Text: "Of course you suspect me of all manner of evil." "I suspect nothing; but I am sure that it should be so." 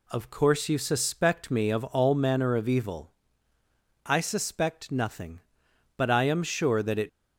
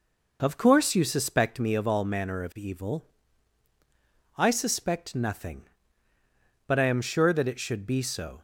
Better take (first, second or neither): second